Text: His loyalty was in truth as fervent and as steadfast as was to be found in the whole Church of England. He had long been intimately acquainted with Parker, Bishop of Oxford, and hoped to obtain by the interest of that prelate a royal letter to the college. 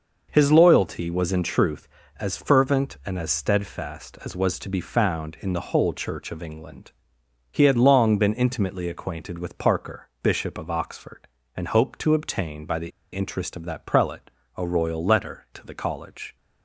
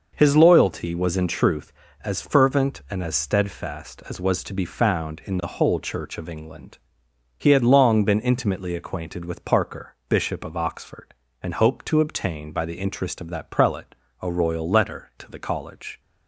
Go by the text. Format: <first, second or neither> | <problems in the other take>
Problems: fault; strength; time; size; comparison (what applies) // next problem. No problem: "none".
second | pauses between "the" and "interest"; slight; at 12.9 s; 0.22 s long // pauses between "prelate" and "a"; slight; at 14.2 s; 0.28 s long; slight in the second